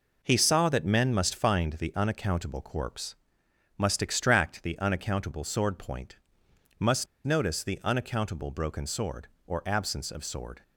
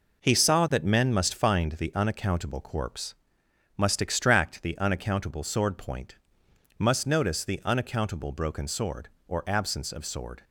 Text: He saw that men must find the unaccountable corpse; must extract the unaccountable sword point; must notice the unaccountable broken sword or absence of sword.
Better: second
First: pauses between "must" and "notice"; slight; at 7.0 s; 0.20 s long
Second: none

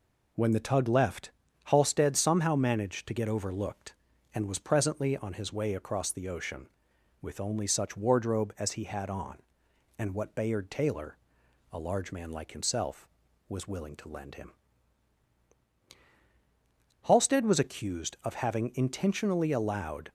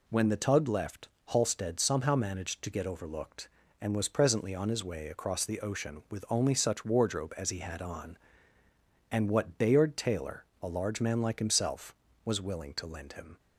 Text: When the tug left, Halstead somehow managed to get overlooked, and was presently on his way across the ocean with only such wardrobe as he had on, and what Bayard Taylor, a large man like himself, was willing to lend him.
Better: second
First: goes on to say "Halstead was accused of having intentionally allowed"; strong; from 17.0 s on; 3.0 s long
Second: none

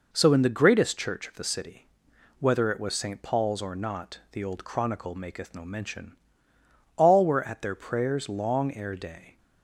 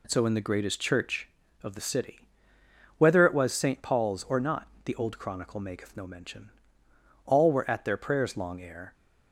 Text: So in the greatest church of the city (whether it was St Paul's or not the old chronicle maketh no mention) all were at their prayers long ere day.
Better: first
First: none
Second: pauses between "not" and "the"; slight; at 4.6 s; 0.16 s long // stops before "day"; at 8.9 s

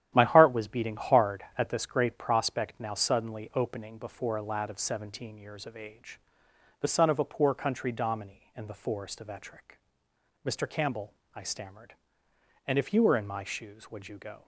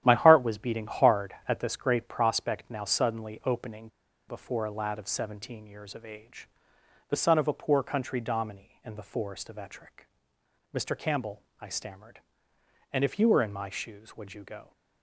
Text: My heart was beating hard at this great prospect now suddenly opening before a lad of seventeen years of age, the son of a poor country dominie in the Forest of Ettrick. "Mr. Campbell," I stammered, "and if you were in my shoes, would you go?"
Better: first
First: starts louder than the rest; strong; until 1.1 s; 11 dB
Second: starts louder than the rest; strong; until 1.0 s; 11 dB // pauses between "opening" and "before"; at 3.8 s; 0.41 s long

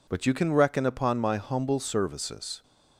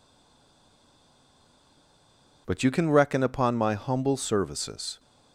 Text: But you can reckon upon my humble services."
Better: first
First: none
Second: stays silent before the first word; until 2.4 s; 2.4 s long

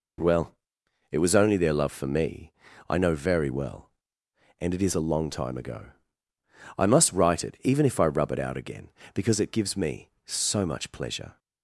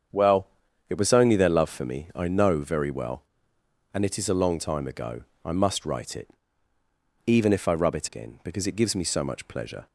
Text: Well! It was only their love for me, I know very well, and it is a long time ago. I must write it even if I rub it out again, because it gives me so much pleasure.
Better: first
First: none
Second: starts louder than the rest; strong; until 1.5 s; 7.5 dB // pauses between "it" and "even"; noticeable; at 6.2 s; 0.98 s long // skips "out"; at 8.0 s

